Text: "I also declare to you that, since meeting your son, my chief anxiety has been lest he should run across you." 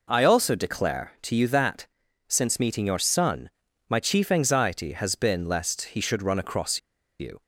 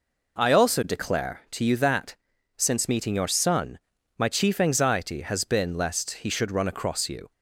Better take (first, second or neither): second